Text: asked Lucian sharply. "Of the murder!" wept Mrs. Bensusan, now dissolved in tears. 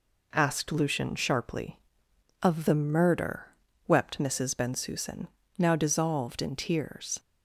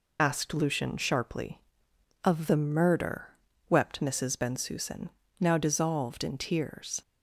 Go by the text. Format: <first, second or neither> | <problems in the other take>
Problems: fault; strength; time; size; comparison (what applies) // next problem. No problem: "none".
first | loses the start of "asked"; at 0.1 s; 55 ms